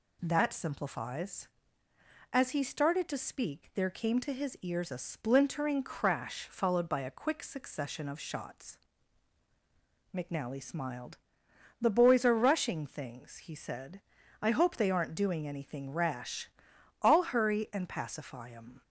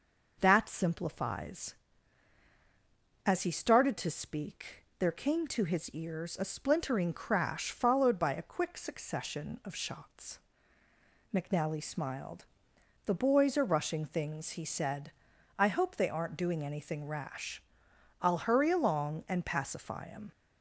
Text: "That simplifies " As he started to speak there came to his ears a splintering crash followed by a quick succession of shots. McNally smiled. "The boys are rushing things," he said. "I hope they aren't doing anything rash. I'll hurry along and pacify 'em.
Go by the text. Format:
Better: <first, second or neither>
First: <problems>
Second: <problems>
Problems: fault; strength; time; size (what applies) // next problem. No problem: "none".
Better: second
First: skips "along"; at 17.7 s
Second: none